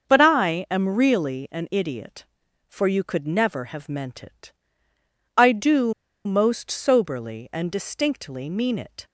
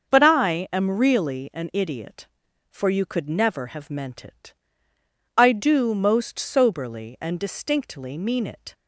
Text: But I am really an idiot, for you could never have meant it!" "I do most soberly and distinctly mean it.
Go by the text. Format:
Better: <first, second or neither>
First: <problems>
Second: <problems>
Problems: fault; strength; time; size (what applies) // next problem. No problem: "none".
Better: second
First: starts louder than the rest; until 1.0 s; 6.5 dB // pauses between "do" and "most"; slight; at 5.9 s; 0.33 s long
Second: starts louder than the rest; until 1.1 s; 6.5 dB